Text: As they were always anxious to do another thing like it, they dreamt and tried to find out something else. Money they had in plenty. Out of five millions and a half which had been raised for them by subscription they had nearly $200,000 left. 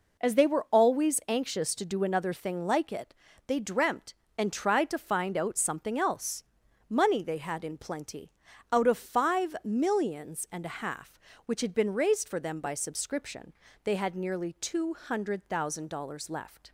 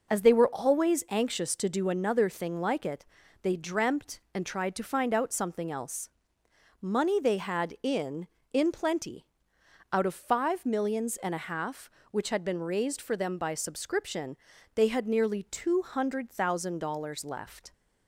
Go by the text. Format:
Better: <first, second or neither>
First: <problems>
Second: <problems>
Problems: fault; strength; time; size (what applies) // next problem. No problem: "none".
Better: first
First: pauses between "subscription" and "they"; slight; at 13.5 s; 0.32 s long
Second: says "in" twice; at 8.5 s // pauses between "subscription" and "they"; at 14.3 s; 0.38 s long